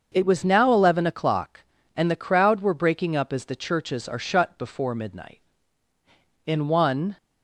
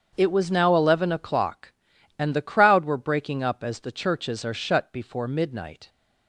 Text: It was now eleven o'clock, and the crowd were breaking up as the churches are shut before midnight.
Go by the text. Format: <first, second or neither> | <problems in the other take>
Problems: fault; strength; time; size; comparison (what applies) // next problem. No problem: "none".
second | starts louder than the rest; until 1.1 s; 6.5 dB; strong in the second // goes on to say "In one"; noticeable; from 6.4 s on; 0.72 s long